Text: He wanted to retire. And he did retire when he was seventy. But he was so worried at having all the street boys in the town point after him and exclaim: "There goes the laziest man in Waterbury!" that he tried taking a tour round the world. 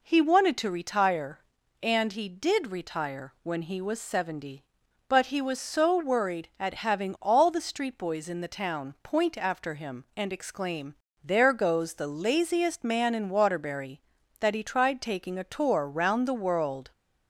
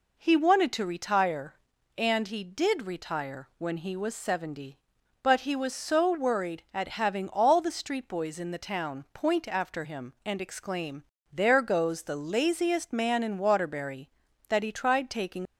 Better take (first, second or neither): first